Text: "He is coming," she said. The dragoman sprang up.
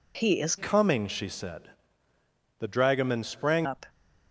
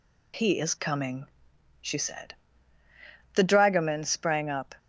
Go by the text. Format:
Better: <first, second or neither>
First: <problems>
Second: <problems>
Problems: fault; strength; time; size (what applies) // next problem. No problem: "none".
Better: second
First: changes voice from "coming" to "sprang"; from 0.5 to 3.6 s; 3.1 s long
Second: none